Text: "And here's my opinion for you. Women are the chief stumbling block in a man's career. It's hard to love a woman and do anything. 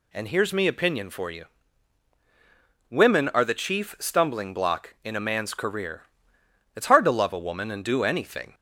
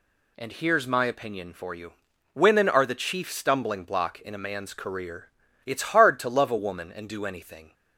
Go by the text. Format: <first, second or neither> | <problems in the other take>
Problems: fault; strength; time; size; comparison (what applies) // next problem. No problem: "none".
second | says "me" for "my"; at 0.5 s